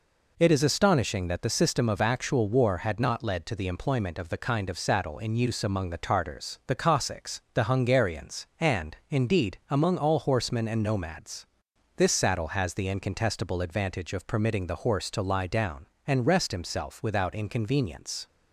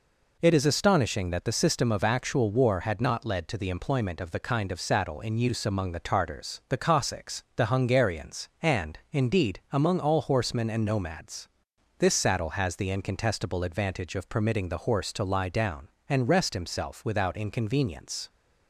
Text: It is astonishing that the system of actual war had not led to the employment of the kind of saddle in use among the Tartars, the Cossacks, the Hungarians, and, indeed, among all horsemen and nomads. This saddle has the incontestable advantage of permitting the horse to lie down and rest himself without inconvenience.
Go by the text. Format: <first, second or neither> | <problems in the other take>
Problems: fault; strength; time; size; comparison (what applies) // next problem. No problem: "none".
neither | none